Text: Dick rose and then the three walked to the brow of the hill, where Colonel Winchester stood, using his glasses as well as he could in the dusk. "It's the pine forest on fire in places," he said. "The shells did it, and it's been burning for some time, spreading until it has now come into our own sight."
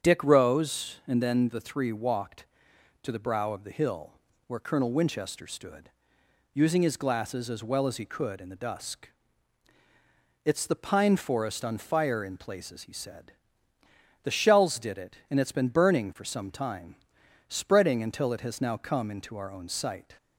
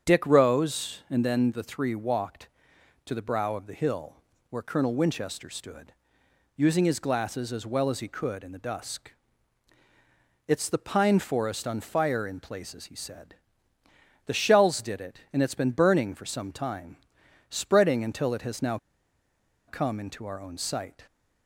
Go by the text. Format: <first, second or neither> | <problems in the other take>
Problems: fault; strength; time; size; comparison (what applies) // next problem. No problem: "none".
first | starts louder than the rest; strong; until 1.1 s; 7 dB; strong in the first // pauses between "now" and "come"; noticeable; at 18.7 s; 0.89 s long